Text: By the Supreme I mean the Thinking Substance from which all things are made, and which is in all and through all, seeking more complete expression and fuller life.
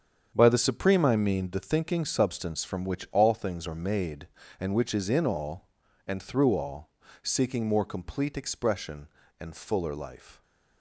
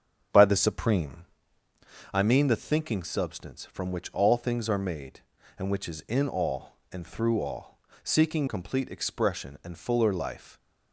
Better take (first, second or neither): first